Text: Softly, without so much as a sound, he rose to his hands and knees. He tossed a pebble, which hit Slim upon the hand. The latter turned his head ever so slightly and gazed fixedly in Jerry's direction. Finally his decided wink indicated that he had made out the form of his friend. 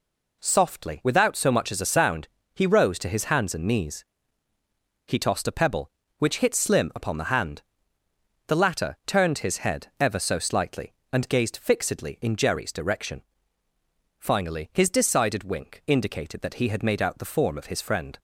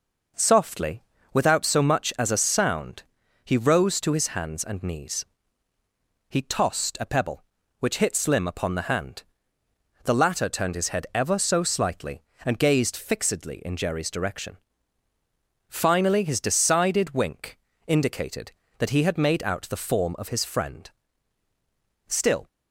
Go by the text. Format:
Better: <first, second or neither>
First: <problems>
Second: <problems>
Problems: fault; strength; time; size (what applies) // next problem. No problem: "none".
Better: first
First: none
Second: pauses between "wink" and "indicated"; slight; at 17.5 s; 0.30 s long // goes on to say "Still"; slight; from 22.0 s on; 0.40 s long